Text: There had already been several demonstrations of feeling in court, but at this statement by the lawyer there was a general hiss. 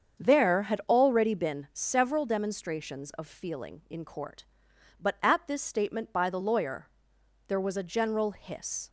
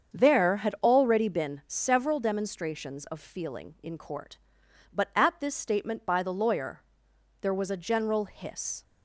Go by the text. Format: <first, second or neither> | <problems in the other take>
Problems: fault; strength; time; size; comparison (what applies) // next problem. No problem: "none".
neither | starts louder than the rest; strong; the same in both // pauses between "lawyer" and "there"; noticeable; the same in both